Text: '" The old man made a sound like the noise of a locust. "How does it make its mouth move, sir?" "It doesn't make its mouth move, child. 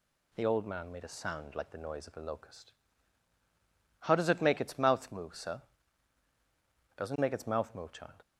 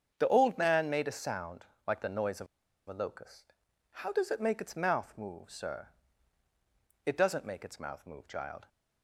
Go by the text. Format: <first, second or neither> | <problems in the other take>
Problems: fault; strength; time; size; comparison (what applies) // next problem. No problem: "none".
first | starts louder than the rest; strong; until 1.1 s; 7.5 dB // pauses between "sound" and "like"; slight; at 1.6 s; 0.22 s long // pauses between "of" and "a"; at 2.4 s; 0.41 s long